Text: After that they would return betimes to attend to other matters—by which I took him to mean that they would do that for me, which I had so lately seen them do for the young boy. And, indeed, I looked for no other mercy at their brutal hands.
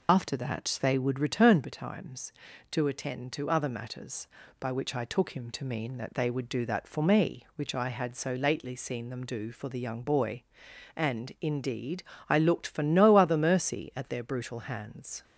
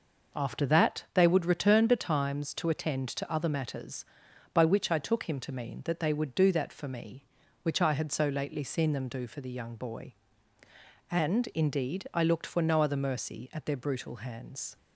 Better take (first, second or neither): second